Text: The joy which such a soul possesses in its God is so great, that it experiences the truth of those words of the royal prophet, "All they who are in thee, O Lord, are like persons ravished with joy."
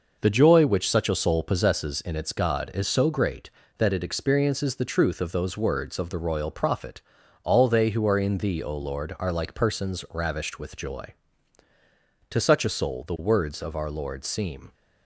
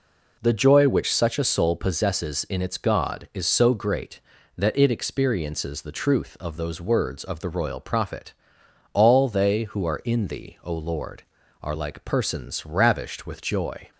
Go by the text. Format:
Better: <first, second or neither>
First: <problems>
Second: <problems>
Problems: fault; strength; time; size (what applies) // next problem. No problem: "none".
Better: second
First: goes on to say "To such a soul the words of our Lord seem"; strong; from 12.3 s on; 2.4 s long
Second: none